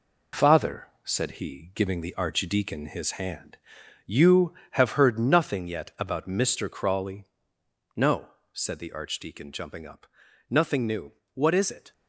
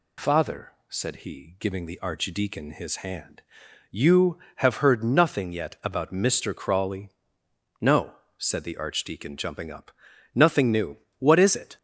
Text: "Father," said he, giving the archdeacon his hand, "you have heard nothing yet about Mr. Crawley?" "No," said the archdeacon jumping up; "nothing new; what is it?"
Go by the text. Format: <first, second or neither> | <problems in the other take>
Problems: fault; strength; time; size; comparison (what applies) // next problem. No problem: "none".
second | gets quieter; noticeable; throughout; 5.5 dB